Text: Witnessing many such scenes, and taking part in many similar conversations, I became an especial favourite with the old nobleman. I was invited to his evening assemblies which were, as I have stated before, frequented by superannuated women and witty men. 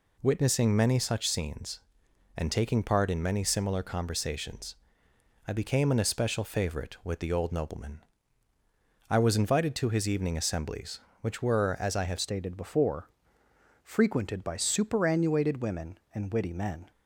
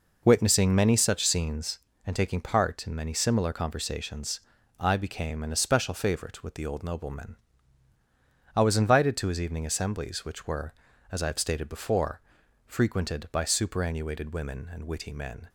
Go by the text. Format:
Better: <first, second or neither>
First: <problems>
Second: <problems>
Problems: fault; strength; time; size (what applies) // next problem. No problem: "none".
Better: second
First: changes voice at "stated"; from 12.1 s on; 4.8 s long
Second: none